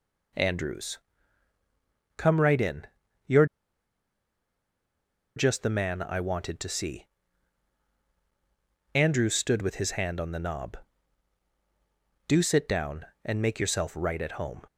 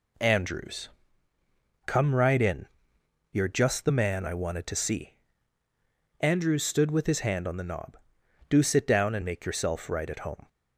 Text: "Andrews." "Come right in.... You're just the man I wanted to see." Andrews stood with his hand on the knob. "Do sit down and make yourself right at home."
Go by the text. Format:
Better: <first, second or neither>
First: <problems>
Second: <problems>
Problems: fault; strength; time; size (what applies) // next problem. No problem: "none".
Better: second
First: pauses between "You're" and "just"; strong; at 3.4 s; 1.9 s long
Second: none